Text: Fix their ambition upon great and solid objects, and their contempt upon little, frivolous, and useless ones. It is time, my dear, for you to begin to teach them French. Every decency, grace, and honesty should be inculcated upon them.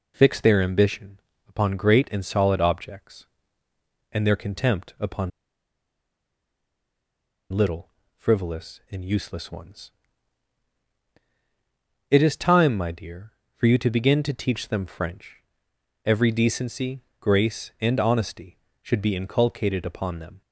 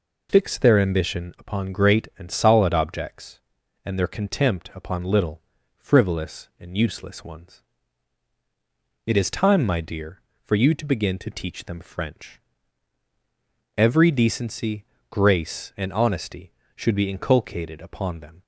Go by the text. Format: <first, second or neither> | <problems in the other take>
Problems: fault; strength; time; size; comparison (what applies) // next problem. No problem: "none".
second | pauses between "ambition" and "upon"; slight; at 1.1 s; 0.26 s long // pauses between "upon" and "little"; strong; at 5.3 s; 2.2 s long